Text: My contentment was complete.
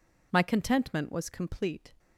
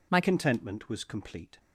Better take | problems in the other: first | changes voice at "contentment"; from 0.2 s on; 1.3 s long

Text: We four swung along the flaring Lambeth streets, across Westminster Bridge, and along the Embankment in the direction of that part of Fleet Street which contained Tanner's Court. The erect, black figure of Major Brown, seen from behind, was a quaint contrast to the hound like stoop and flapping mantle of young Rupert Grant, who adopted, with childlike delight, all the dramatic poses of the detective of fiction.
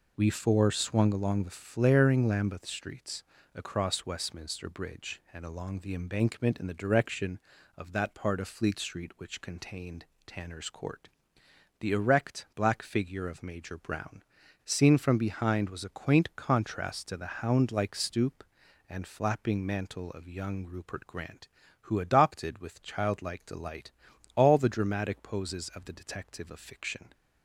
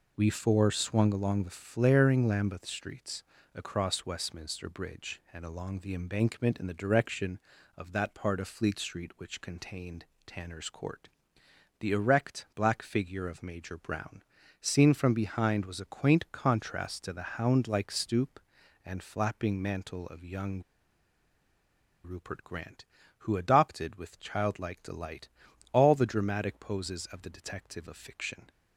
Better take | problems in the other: first | pauses between "contained" and "Tanner's"; slight; at 10.0 s; 0.22 s long; slight in the first // pauses between "young" and "Rupert"; strong; at 20.6 s; 1.4 s long

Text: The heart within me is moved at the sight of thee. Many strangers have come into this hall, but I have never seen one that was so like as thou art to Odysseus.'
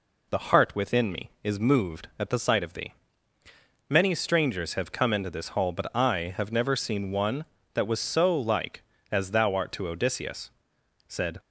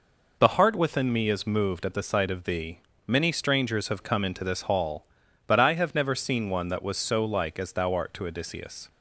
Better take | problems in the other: second | goes on to say "Said"; slight; from 11.0 s on; 0.32 s long

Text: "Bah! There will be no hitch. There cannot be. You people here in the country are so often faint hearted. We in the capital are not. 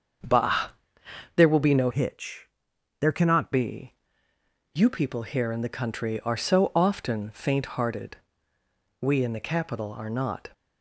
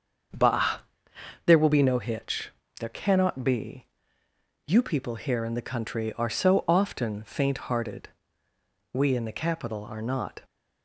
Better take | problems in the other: second | starts louder than the rest; until 1.9 s; 7 dB; also in the second // changes voice from "hitch" to "cannot"; from 1.9 to 3.5 s; 1.6 s long

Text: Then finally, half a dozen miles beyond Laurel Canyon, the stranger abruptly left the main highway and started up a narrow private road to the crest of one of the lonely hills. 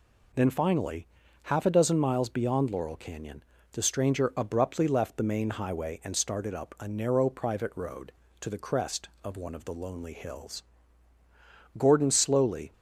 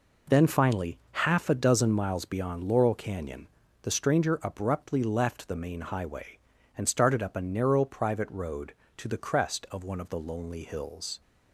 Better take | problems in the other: second | goes on to say "Gordon slowly"; noticeable; from 11.7 s on; 0.94 s long

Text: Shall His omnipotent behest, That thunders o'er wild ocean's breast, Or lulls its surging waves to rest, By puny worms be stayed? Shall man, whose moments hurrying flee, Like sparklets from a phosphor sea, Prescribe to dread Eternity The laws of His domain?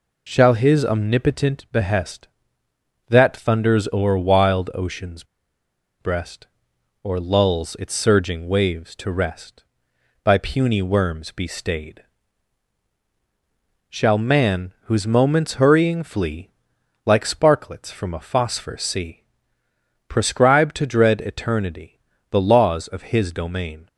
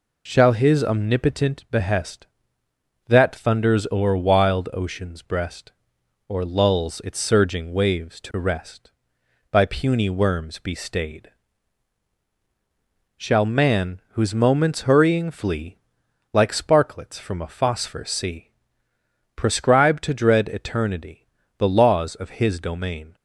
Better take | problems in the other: second | pauses between "ocean's" and "breast"; noticeable; at 5.2 s; 0.76 s long // pauses between "Eternity" and "The"; slight; at 21.9 s; 0.32 s long; slight in the second

